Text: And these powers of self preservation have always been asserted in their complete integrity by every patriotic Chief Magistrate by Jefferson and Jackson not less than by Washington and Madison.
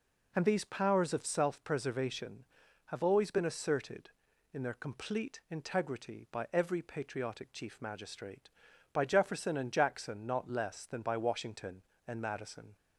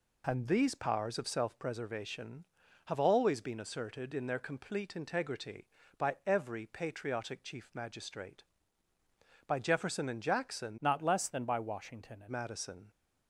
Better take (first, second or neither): first